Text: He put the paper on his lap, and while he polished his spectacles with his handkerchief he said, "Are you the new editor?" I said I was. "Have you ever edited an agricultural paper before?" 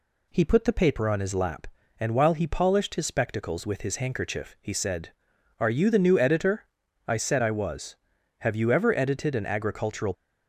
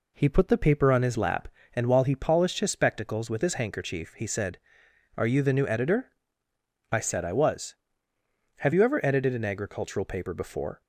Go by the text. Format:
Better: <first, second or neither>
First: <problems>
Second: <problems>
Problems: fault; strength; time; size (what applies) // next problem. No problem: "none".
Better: second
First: stops before "paper before"; at 10.1 s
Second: none